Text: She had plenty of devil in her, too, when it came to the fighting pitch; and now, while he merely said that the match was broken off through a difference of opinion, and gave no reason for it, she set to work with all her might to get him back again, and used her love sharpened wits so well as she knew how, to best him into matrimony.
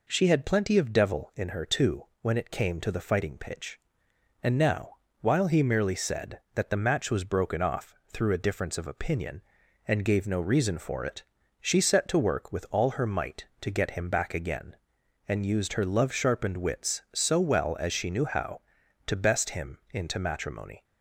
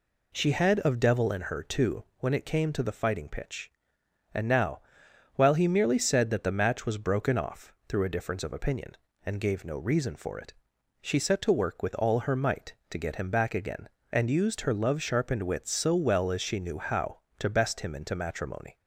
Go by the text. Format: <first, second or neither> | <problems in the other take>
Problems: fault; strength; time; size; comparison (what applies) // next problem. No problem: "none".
first | skips "plenty"; at 0.8 s